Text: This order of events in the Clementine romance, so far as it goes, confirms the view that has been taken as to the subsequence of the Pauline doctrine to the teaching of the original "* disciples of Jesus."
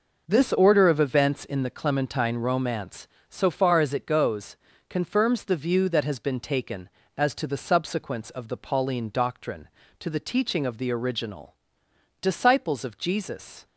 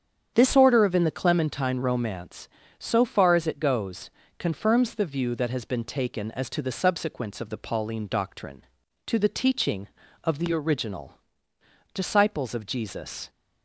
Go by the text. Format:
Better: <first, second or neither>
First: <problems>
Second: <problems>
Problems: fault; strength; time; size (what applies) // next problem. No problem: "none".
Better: first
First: none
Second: starts louder than the rest; strong; until 1.3 s; 8 dB // skips "events"; at 0.9 s